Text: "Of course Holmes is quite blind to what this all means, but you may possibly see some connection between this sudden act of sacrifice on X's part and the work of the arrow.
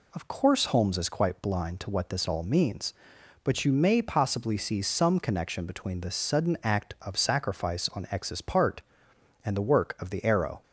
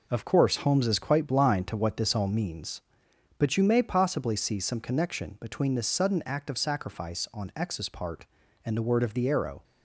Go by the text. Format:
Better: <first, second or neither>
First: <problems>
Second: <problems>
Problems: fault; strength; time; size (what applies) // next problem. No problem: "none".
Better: first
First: none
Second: says "word" for "work"; at 8.8 s